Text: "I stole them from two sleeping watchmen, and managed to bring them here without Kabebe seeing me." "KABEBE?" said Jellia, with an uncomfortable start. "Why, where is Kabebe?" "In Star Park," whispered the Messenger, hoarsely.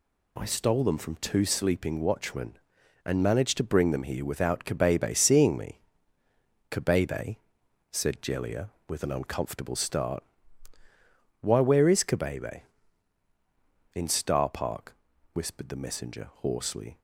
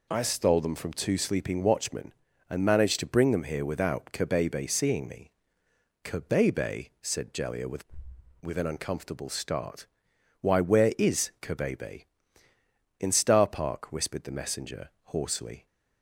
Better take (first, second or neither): first